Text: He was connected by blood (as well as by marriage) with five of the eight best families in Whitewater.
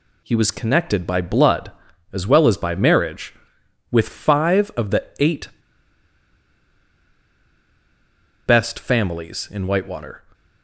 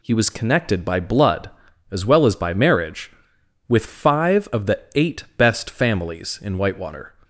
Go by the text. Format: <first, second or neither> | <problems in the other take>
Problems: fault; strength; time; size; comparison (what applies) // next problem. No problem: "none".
second | pauses between "the" and "eight"; slight; at 5.0 s; 0.16 s long; slight in the second // pauses between "eight" and "best"; strong; at 5.4 s; 2.9 s long